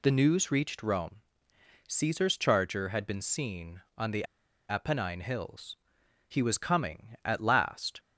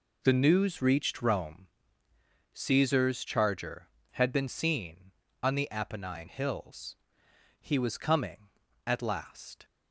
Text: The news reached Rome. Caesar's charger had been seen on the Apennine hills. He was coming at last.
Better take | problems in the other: second | pauses between "the" and "Apennine"; at 4.2 s; 0.45 s long

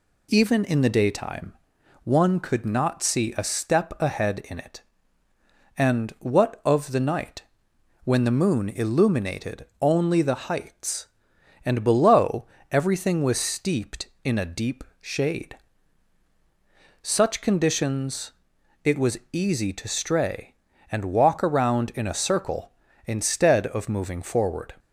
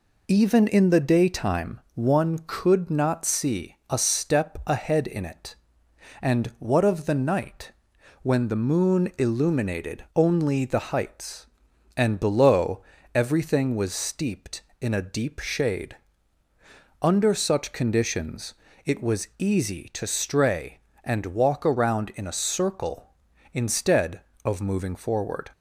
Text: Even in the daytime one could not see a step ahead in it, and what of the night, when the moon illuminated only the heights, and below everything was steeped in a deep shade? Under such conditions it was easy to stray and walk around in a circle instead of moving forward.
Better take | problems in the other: second | pauses between "daytime" and "one"; noticeable; at 1.5 s; 0.50 s long // pauses between "illuminated" and "only"; slight; at 9.6 s; 0.16 s long // pauses between "below" and "everything"; slight; at 12.4 s; 0.24 s long; slight in the second // pauses between "deep" and "shade"; slight; at 14.8 s; 0.18 s long // skips "Under"; at 16.2 s // pauses between "conditions" and "it"; noticeable; at 18.3 s; 0.52 s long; slight in the second

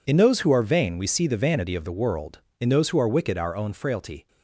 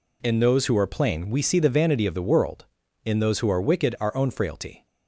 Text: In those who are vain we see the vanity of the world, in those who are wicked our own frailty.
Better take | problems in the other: first | says "plain" for "vain"; at 0.8 s

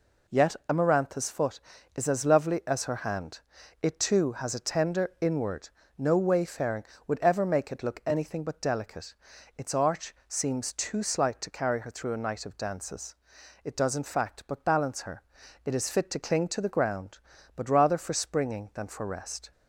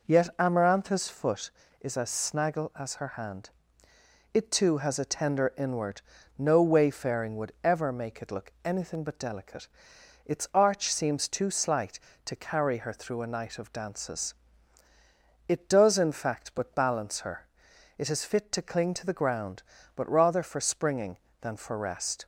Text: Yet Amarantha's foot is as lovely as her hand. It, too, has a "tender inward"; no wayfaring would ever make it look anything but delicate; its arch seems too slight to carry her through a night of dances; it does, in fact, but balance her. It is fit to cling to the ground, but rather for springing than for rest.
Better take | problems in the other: first | says "snaggle" for "lovely"; at 2.0 s

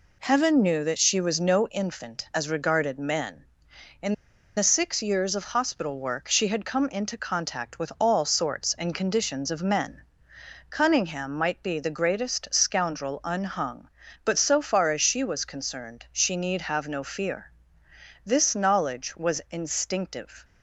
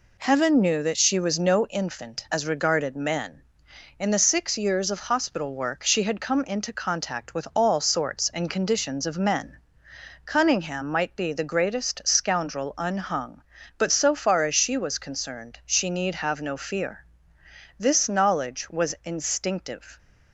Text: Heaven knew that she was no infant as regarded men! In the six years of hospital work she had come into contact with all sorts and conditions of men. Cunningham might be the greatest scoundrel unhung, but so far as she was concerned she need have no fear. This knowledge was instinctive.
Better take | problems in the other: second | pauses between "In" and "the"; at 4.1 s; 0.42 s long

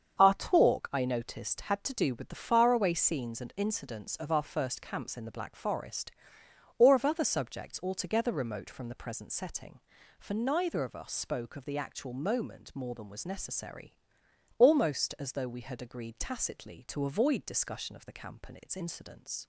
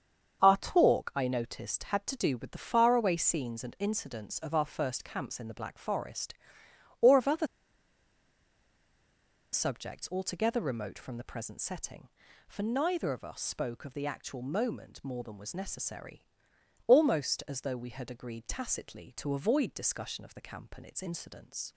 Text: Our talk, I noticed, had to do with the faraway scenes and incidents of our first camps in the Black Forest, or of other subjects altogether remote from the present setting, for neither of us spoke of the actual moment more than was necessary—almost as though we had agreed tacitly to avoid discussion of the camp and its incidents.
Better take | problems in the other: first | starts louder than the rest; strong; until 1.4 s; 7 dB; strong in the first // pauses between "other" and "subjects"; strong; at 7.4 s; 2.0 s long

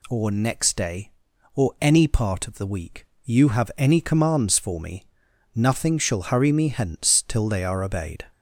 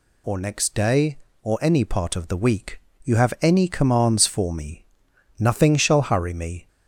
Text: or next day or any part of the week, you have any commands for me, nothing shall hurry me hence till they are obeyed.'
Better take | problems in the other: first | stops before "hence till they are obeyed"; at 6.6 s

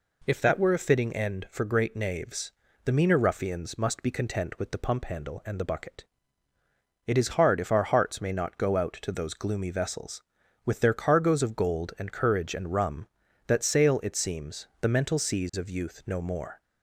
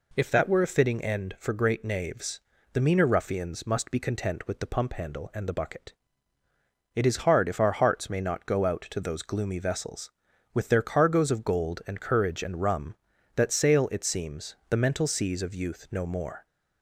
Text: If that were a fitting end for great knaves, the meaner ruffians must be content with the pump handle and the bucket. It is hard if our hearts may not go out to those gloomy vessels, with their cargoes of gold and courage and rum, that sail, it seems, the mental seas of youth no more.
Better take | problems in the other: neither | none

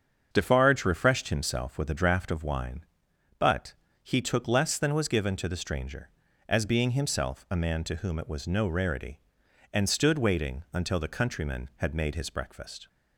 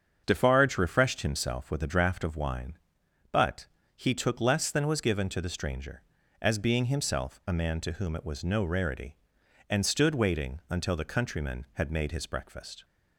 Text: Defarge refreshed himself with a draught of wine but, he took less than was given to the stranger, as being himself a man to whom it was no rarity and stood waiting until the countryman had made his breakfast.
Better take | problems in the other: neither | starts louder than the rest; the same in both

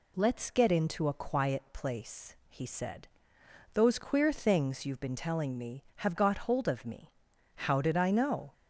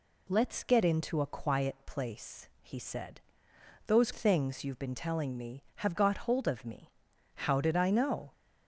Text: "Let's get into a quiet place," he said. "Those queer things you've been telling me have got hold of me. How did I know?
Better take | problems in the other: first | skips "queer"; at 4.1 s

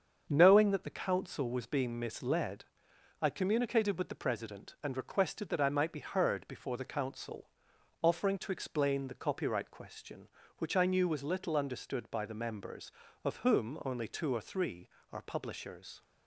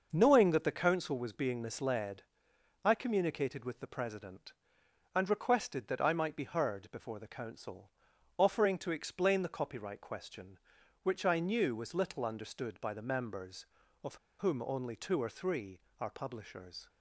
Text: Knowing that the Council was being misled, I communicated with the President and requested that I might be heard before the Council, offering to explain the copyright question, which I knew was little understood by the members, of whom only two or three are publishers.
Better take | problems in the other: first | starts louder than the rest; noticeable; until 1.1 s; 6 dB; also in the first // pauses between "of" and "whom"; slight; at 14.1 s; 0.24 s long

